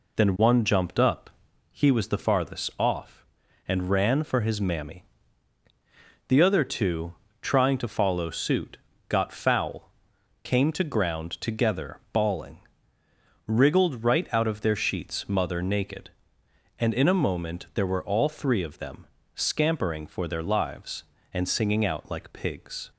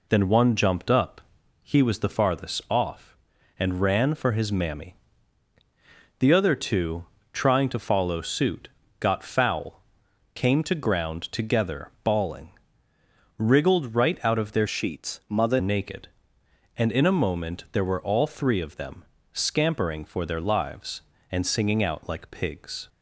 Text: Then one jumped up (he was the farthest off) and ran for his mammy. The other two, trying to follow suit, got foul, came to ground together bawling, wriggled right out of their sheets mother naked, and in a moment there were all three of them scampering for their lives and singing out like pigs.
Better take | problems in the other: first | changes voice from "sheets" to "mother"; from 14.6 to 15.5 s; 0.9 s long // pauses between "them" and "scampering"; slight; at 19.0 s; 0.28 s long; slight in the first

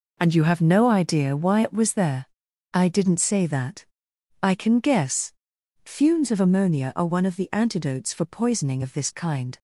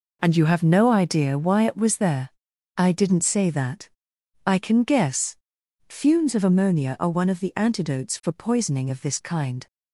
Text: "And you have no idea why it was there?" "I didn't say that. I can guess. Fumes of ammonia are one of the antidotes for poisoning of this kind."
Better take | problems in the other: neither | none

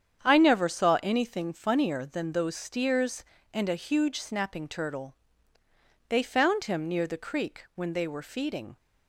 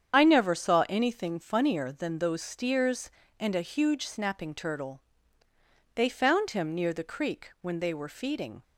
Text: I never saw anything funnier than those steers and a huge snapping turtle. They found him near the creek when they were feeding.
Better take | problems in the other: first | loses the start of "I"; at 0.1 s; 60 ms // starts louder than the rest; strong; until 1.1 s; 8 dB; strong in the first

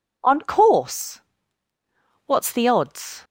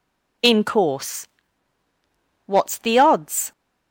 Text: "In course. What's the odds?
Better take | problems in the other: second | says "On" for "In"; at 0.2 s

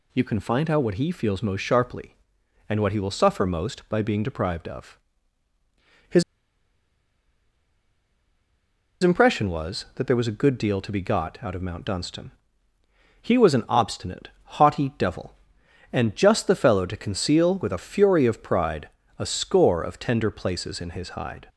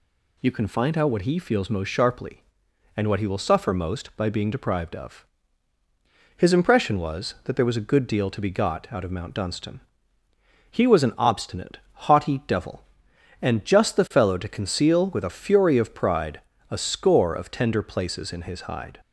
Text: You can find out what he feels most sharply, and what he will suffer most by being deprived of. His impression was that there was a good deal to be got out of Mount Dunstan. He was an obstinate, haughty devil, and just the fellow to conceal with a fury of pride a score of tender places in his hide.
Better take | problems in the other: second | pauses between "His" and "impression"; strong; at 6.2 s; 2.8 s long // pauses between "pride" and "a"; slight; at 18.8 s; 0.30 s long; slight in the second

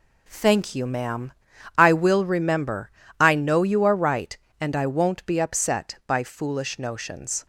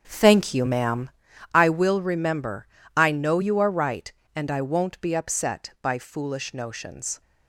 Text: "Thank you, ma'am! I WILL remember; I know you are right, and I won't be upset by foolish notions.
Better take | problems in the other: first | starts louder than the rest; until 1.3 s; 7 dB

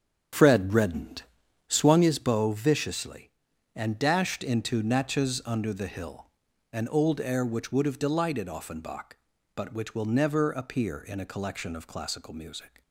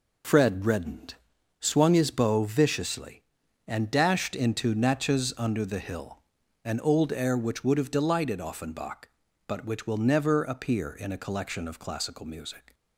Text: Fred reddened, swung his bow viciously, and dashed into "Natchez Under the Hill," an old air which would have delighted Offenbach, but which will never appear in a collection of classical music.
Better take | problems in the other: second | starts louder than the rest; strong; until 2.1 s; 8 dB

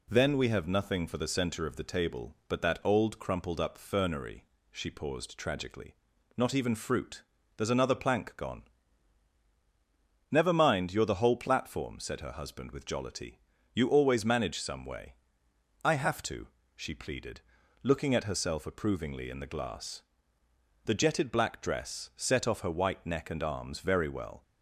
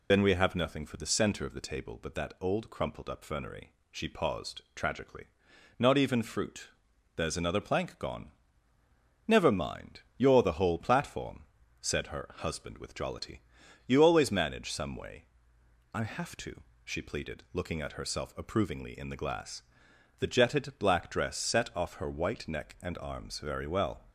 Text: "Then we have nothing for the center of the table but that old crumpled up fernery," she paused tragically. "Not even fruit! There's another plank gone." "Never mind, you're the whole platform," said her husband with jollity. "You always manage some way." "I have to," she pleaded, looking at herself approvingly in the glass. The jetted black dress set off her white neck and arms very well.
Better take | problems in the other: first | loses the start of "Then"; at 0.1 s; 80 ms

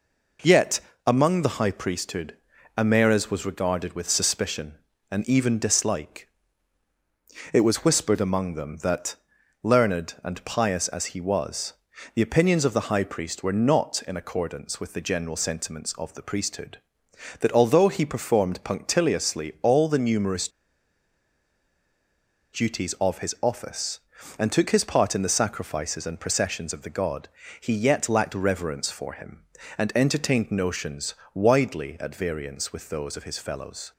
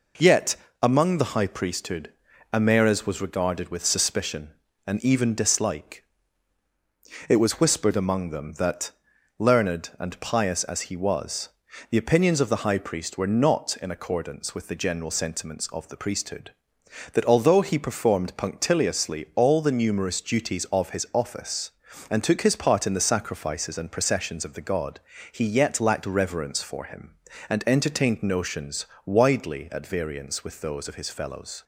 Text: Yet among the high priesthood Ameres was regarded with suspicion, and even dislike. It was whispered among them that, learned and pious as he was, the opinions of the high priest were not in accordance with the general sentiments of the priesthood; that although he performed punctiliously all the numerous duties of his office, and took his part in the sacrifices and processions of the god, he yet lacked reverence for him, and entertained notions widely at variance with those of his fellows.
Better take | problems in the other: second | pauses between "Yet" and "among"; slight; at 0.8 s; 0.26 s long; slight in the second // pauses between "priesthood" and "Ameres"; at 2.3 s; 0.40 s long; also in the second // pauses between "numerous" and "duties"; strong; at 20.4 s; 2.0 s long // pauses between "notions" and "widely"; slight; at 31.1 s; 0.20 s long; slight in the second

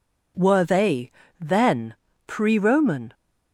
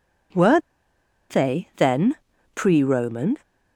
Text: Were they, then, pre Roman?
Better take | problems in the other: first | pauses between "Were" and "they"; noticeable; at 0.6 s; 0.69 s long

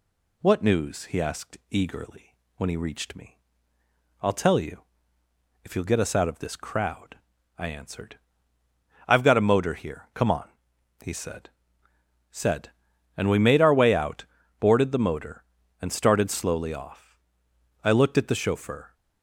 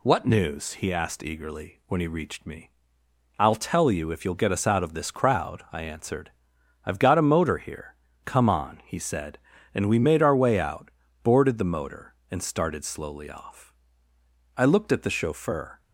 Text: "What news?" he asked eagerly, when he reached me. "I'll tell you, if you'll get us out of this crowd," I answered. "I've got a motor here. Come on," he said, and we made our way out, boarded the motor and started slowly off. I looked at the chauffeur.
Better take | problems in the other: second | says "said" twice; at 12.2 s

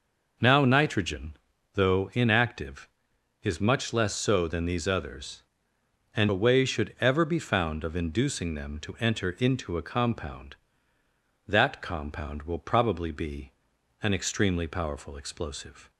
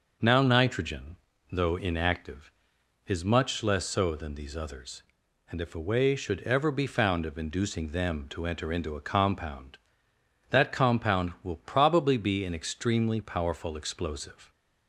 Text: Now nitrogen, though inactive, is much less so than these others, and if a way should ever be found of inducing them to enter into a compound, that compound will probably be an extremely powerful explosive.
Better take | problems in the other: second | skips "if"; at 6.2 s // pauses between "be" and "an"; noticeable; at 13.5 s; 0.50 s long

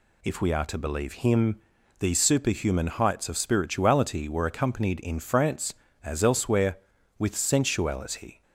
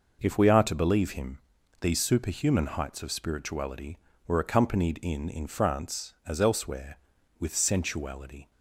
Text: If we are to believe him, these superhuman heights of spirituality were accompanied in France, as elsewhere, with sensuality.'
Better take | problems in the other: first | says "in" twice; at 5.2 s

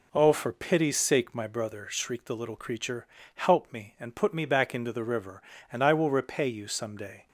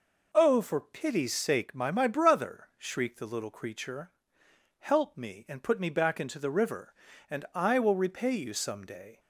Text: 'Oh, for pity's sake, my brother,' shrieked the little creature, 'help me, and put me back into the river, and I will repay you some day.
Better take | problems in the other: first | says "my" twice; at 1.9 s

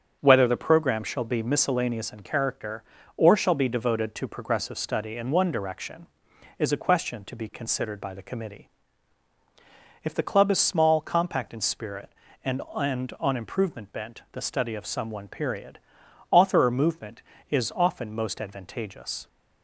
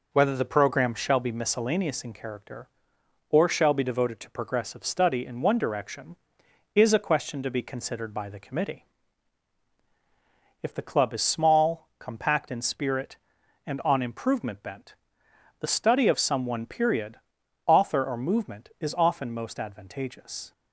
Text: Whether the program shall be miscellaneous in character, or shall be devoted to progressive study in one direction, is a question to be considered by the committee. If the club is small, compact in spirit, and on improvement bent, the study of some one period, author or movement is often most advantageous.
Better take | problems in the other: second | starts louder than the rest; until 1.2 s; 7 dB // says "and" twice; at 12.7 s

